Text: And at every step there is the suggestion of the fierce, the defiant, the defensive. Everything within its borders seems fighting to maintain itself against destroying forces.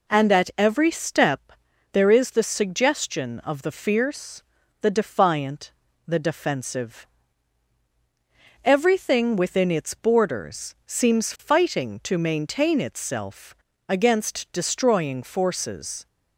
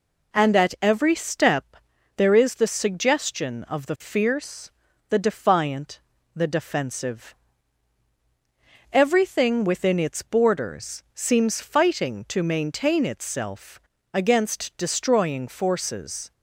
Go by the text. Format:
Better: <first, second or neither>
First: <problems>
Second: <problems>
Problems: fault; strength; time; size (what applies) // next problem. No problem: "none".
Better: neither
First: pauses between "step" and "there"; at 1.5 s; 0.42 s long // pauses between "itself" and "against"; slight; at 13.5 s; 0.34 s long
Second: pauses between "step" and "there"; at 1.7 s; 0.42 s long // pauses between "itself" and "against"; slight; at 13.7 s; 0.34 s long